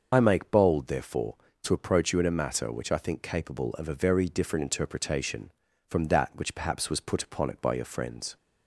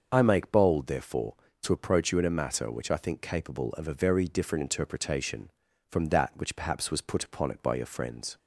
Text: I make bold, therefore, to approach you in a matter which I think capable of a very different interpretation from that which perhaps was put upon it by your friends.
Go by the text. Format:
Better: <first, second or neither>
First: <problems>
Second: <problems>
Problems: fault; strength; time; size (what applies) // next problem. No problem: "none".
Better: second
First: loses the start of "I"; at 0.1 s; 30 ms // starts louder than the rest; until 1.1 s; 6 dB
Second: starts louder than the rest; until 1.1 s; 6.5 dB